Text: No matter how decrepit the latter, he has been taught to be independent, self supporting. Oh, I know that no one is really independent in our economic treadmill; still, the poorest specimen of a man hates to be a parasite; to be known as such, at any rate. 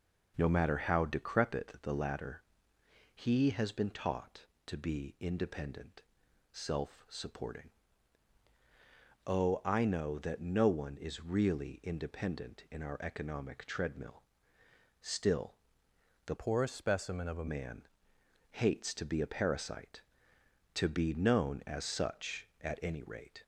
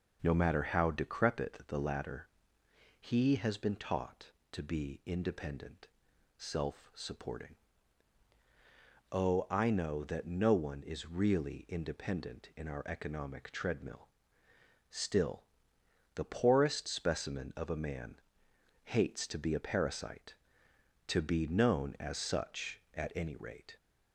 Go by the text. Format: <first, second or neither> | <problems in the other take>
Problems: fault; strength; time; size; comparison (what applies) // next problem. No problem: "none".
second | changes voice from "poorest" to "a"; from 16.3 to 17.4 s; 1.1 s long // pauses between "man" and "hates"; noticeable; at 17.8 s; 0.68 s long; noticeable in the second